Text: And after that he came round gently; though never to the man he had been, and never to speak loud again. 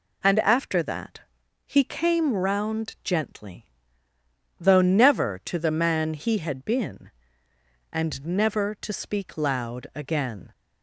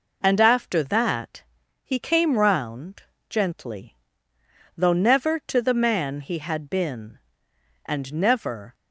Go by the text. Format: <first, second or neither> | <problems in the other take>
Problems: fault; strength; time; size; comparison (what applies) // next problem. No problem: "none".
first | pauses between "that" and "he"; at 1.4 s; 0.42 s long; also in the first // pauses between "round" and "gently"; slight; at 3.0 s; 0.26 s long // stops before "to speak loud again"; at 8.7 s